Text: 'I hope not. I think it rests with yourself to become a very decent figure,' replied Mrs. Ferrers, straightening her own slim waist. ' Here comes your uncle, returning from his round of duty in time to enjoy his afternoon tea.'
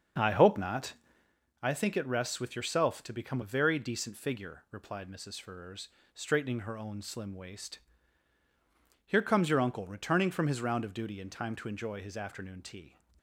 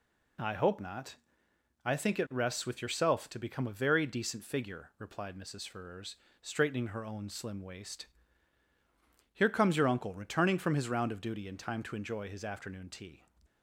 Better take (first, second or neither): second